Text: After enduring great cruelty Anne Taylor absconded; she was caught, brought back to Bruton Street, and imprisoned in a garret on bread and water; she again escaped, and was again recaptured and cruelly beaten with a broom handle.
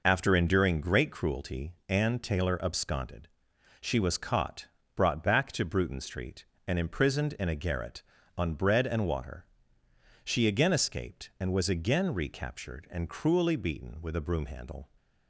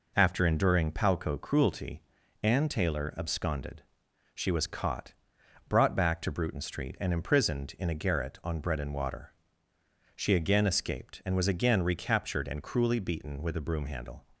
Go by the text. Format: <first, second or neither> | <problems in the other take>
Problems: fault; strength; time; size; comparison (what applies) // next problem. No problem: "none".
first | says "palco" for "great"; at 0.9 s // pauses between "cruelty" and "Anne"; at 2.0 s; 0.40 s long